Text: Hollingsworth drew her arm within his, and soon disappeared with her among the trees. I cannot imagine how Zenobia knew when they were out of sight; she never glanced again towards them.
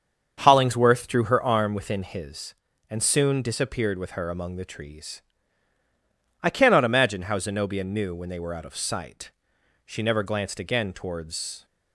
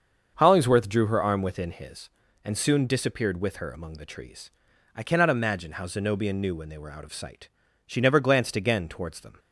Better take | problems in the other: second | starts louder than the rest; strong; until 1.3 s; 7 dB; also in the second // stops before "them"; at 11.6 s

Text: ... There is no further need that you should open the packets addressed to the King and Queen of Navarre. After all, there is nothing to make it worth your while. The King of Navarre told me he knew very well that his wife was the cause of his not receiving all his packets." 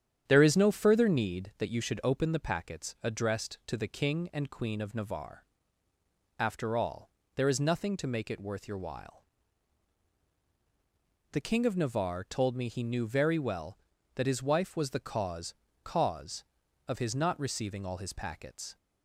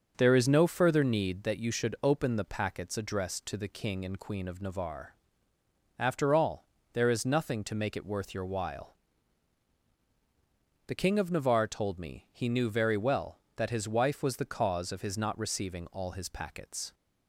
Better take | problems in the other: second | starts louder than the rest; strong; until 1.2 s; 9.5 dB; also in the second // says "cause" twice; at 15.8 s

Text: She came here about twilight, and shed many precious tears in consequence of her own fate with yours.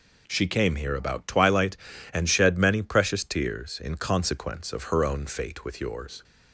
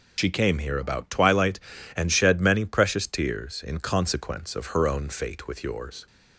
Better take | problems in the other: first | loses the start of "She"; at 0.1 s; 80 ms

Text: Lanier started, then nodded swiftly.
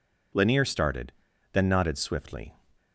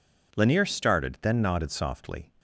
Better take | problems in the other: first | says "softly" for "swiftly"; at 1.7 s

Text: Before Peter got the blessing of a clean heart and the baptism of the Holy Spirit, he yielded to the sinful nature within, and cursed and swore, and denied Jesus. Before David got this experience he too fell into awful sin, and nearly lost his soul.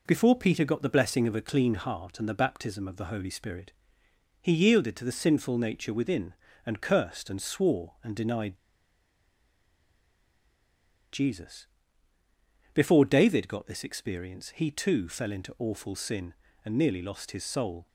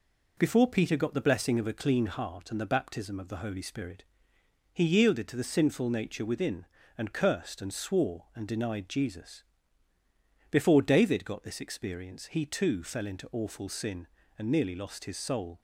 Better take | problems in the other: second | pauses between "denied" and "Jesus"; strong; at 8.5 s; 2.5 s long

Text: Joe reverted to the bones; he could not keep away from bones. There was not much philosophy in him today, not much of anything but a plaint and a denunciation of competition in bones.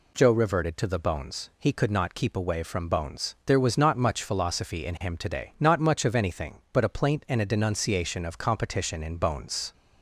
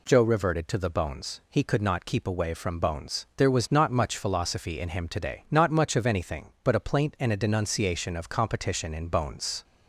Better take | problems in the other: neither | none

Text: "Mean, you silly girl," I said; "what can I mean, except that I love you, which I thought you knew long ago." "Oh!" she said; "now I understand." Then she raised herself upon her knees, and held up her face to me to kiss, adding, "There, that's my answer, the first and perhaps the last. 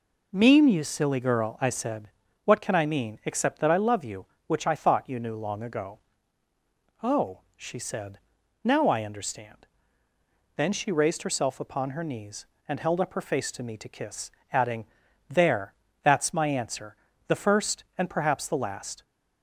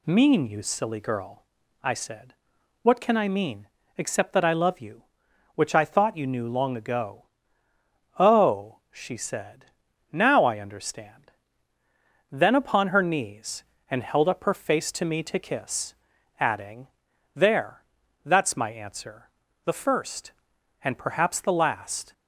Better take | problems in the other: first | skips "she raised herself"; at 12.5 s

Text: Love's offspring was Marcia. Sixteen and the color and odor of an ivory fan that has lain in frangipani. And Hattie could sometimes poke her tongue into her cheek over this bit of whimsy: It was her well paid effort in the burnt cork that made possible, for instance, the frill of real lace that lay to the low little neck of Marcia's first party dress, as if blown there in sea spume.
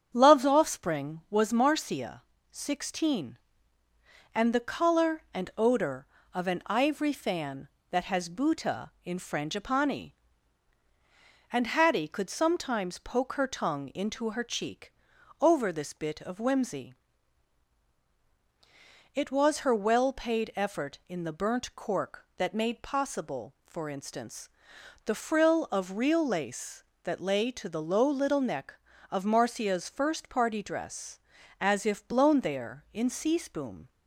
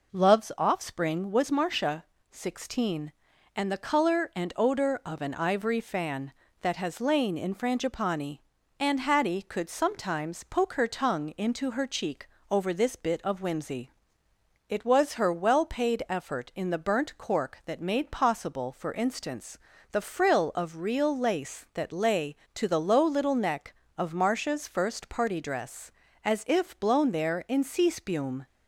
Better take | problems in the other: second | starts louder than the rest; strong; until 1.1 s; 8 dB // says "buta" for "lain"; at 8.2 s // pauses between "cheek" and "over"; noticeable; at 14.9 s; 0.48 s long; slight in the second

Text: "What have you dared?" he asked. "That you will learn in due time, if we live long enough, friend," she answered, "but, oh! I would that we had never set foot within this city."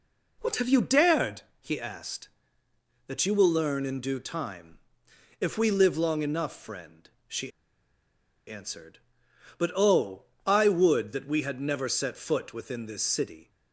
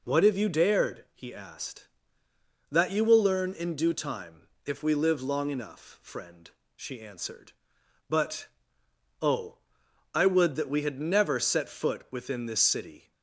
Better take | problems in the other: second | pauses between "she" and "answered"; noticeable; at 7.5 s; 0.97 s long

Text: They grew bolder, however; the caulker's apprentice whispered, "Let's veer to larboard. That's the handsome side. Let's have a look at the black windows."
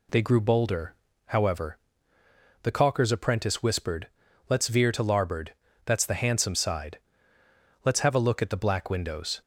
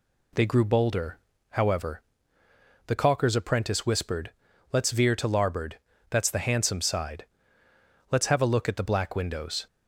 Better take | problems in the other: neither | none

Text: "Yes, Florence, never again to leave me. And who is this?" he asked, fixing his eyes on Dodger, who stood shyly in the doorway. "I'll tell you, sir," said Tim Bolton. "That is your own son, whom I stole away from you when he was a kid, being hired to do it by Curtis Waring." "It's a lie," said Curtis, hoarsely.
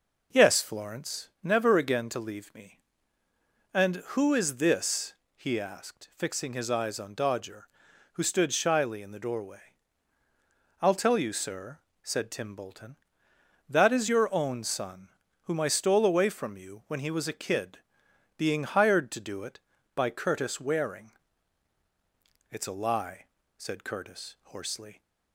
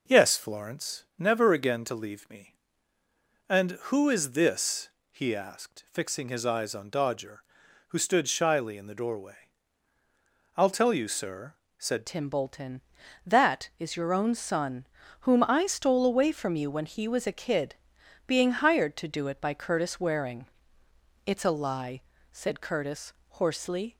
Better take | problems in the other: first | changes voice at "Tim"; from 12.0 s on; 11.9 s long

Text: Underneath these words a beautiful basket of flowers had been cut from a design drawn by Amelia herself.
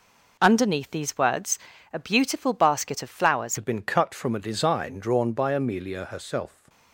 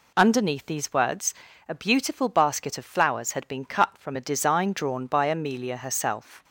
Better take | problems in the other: second | pauses between "words" and "a"; slight; at 1.5 s; 0.34 s long; slight in the second // changes voice at "had"; from 3.5 s on; 3.1 s long

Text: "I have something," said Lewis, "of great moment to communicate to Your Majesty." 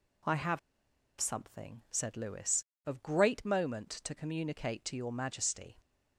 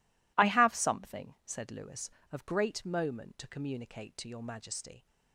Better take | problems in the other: second | pauses between "have" and "something"; noticeable; at 0.5 s; 0.60 s long

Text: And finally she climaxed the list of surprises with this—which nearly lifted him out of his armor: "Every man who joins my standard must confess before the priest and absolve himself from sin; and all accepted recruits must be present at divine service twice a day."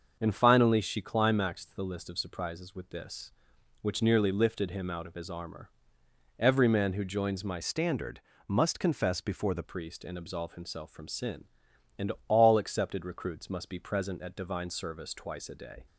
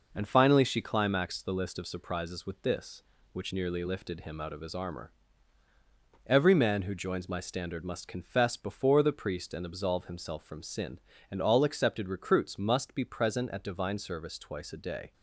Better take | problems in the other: second | starts louder than the rest; until 1.2 s; 6.5 dB // changes voice from "standard" to "the"; from 7.6 to 9.6 s; 2.0 s long // pauses between "standard" and "must"; slight; at 8.1 s; 0.28 s long // pauses between "and" and "all"; slight; at 12.1 s; 0.16 s long

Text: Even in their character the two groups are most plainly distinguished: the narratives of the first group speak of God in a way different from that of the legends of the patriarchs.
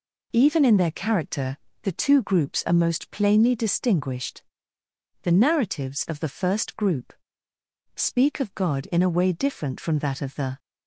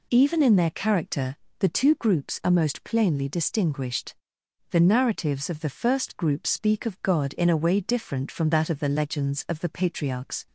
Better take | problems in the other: second | pauses between "character" and "the"; slight; at 1.5 s; 0.26 s long; slight in the second // pauses between "group" and "speak"; noticeable; at 7.1 s; 0.82 s long // stops before "legends of the patriarchs"; at 10.5 s

